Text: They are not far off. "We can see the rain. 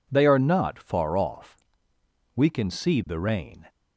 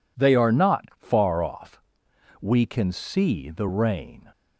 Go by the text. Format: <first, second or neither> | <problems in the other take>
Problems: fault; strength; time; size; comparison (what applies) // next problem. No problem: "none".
neither | none